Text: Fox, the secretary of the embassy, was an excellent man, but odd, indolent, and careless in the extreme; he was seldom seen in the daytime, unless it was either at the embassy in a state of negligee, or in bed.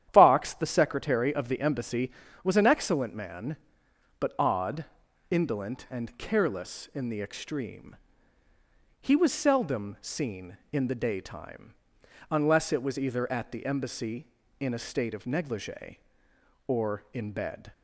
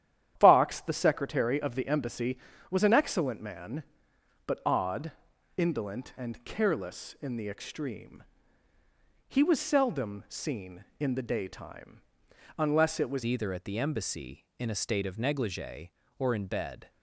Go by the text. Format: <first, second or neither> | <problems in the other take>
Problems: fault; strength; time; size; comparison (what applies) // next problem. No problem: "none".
first | starts louder than the rest; strong; until 1.3 s; 10.5 dB; strong in the first // changes voice at "either"; from 13.2 s on; 3.6 s long